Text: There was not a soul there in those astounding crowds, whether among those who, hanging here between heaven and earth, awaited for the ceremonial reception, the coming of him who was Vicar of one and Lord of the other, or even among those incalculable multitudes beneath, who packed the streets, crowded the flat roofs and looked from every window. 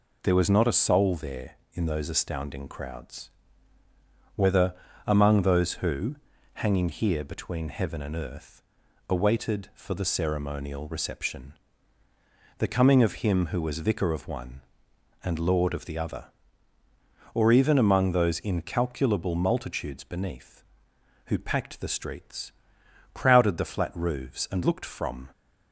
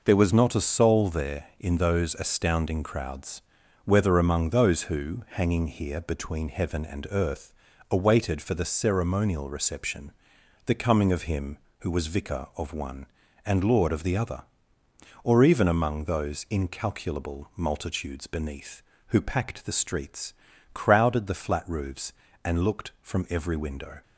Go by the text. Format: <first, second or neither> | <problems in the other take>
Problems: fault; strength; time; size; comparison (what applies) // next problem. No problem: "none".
second | pauses between "whether" and "among"; slight; at 4.7 s; 0.32 s long // stops before "every window"; at 25.3 s